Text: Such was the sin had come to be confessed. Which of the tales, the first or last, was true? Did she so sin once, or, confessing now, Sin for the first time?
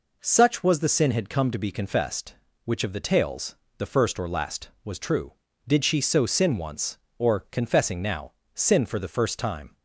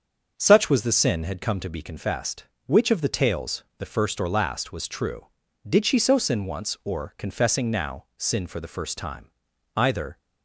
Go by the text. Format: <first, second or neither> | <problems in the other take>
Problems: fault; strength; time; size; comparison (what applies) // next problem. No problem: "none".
first | starts louder than the rest; until 1.3 s; 6.5 dB // goes on to say "Either"; slight; from 9.7 s on; 0.42 s long